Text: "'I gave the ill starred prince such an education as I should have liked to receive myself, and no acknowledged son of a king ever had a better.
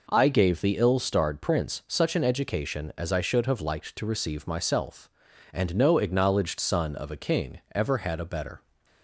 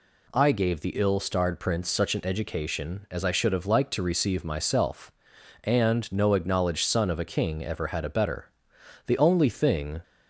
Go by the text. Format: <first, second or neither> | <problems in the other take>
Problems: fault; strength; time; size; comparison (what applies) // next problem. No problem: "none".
first | goes on to say "The only thing"; noticeable; from 9.0 s on; 0.96 s long